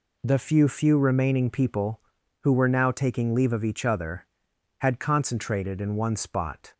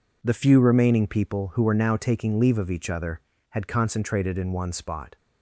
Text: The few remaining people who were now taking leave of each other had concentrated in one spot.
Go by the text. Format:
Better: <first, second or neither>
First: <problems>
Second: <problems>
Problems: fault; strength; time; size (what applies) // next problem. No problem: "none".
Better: second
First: says "few" twice; at 0.6 s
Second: none